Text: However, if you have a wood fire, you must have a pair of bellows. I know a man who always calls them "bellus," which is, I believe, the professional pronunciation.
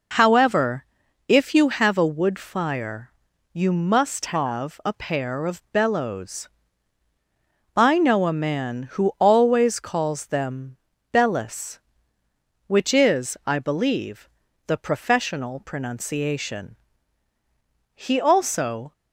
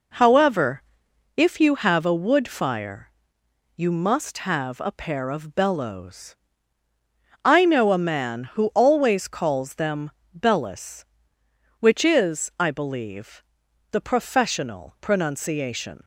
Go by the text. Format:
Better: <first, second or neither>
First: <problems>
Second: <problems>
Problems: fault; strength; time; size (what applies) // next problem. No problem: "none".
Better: second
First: pauses between "them" and "bellus"; at 10.7 s; 0.38 s long // goes on to say "He also"; noticeable; from 17.9 s on; 0.96 s long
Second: pauses between "them" and "bellus"; slight; at 10.0 s; 0.28 s long